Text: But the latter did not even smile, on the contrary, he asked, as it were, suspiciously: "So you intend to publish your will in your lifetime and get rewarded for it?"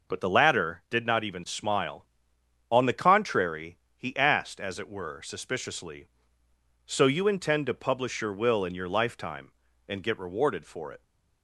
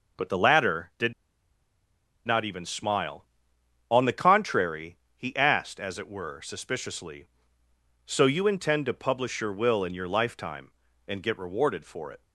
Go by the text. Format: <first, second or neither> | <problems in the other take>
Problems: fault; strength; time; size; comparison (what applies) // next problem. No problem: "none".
first | pauses between "did" and "not"; at 1.1 s; 1.1 s long